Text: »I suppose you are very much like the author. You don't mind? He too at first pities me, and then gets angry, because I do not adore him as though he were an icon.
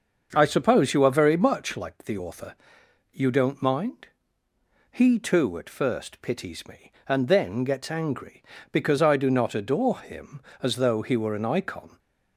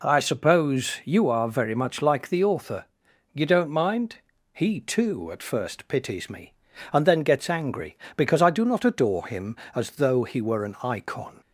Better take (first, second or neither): second